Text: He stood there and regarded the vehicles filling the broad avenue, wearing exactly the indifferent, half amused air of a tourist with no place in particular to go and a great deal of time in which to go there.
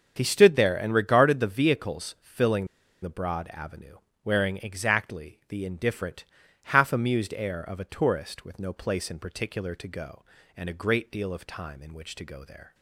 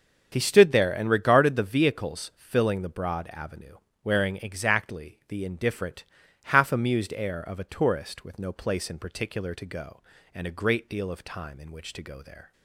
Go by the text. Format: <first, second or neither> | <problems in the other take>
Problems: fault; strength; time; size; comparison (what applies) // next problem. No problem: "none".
second | starts louder than the rest; until 1.1 s; 6.5 dB; also in the second // pauses between "filling" and "the"; at 2.6 s; 0.37 s long